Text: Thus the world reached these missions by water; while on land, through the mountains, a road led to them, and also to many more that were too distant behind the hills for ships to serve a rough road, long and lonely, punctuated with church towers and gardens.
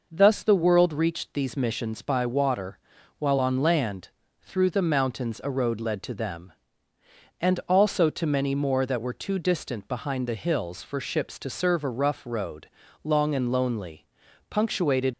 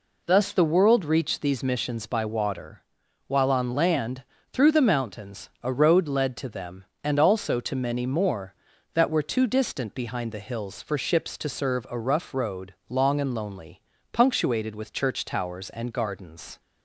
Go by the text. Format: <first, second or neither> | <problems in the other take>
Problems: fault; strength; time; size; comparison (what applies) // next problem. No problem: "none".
second | stops before "with church towers and gardens"; at 15.1 s